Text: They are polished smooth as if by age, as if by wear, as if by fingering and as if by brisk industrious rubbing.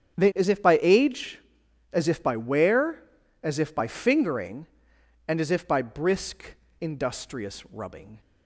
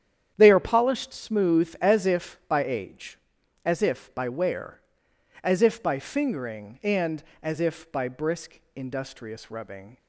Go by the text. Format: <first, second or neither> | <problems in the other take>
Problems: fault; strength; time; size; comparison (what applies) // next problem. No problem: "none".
second | starts louder than the rest; strong; until 1.2 s; 8.5 dB; strong in the second // skips "are polished smooth"; at 0.3 s // pauses between "brisk" and "industrious"; slight; at 6.5 s; 0.24 s long; slight in the second